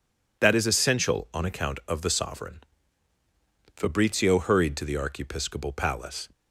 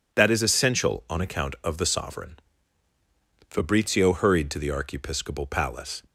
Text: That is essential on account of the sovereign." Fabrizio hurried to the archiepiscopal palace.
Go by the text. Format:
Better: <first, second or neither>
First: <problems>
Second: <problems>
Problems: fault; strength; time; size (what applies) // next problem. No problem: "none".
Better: neither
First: none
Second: none